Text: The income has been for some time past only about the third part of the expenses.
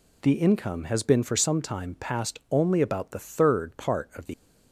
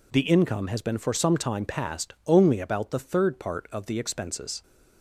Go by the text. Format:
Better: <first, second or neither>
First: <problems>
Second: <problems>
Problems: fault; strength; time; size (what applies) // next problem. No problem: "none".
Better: second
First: stops before "expenses"; at 4.3 s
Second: none